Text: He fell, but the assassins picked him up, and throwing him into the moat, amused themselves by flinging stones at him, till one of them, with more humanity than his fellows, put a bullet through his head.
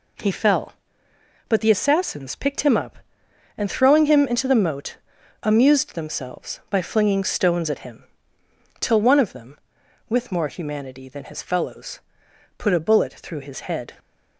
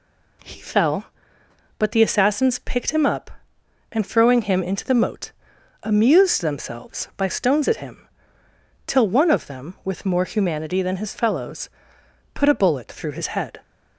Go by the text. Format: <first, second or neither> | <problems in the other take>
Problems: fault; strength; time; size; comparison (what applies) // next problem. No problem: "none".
first | skips "flinging"; at 7.2 s